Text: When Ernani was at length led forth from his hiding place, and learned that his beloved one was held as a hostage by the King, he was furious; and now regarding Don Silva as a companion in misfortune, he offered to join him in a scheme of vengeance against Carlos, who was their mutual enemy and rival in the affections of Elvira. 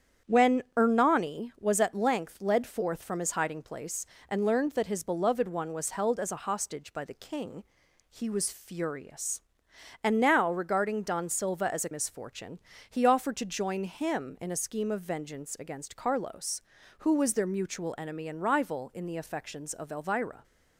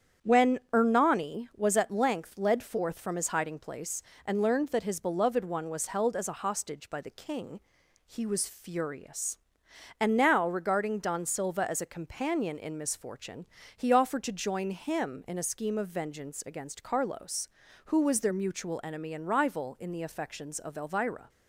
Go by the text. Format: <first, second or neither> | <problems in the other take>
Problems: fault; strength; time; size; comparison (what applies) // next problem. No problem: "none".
second | starts louder than the rest; strong; until 1.4 s; 8.5 dB; strong in the second // skips "companion in"; at 11.9 s